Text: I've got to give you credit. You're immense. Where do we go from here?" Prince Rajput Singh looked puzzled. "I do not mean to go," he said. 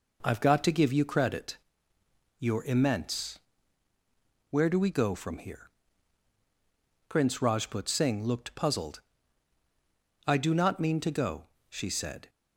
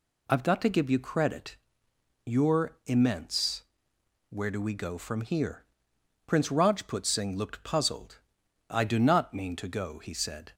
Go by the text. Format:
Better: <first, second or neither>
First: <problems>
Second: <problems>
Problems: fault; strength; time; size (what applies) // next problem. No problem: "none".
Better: second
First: says "she" for "he"; at 11.6 s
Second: none